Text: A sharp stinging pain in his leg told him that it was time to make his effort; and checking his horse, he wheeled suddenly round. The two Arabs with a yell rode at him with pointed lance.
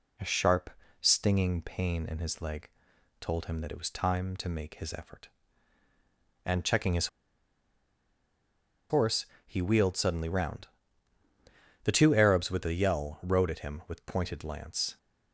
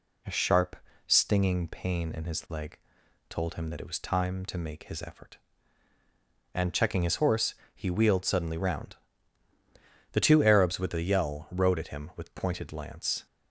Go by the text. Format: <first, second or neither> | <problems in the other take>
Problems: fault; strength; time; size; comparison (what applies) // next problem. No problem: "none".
second | pauses between "sharp" and "stinging"; slight; at 0.7 s; 0.30 s long; slight in the second // pauses between "leg" and "told"; noticeable; at 2.6 s; 0.52 s long; noticeable in the second // pauses between "his" and "horse"; strong; at 7.0 s; 1.8 s long